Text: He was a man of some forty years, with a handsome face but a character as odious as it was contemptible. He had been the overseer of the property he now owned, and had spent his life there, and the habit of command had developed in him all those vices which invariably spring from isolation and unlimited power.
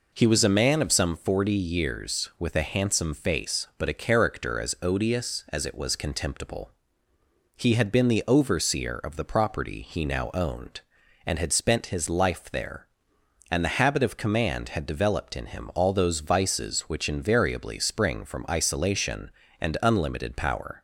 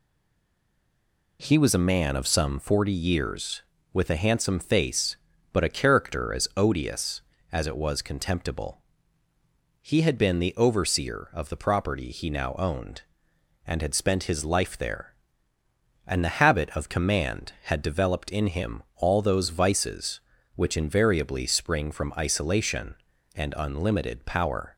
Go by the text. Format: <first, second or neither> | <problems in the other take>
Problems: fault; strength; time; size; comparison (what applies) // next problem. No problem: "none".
first | stays silent before the first word; noticeable; until 1.3 s; 1.3 s long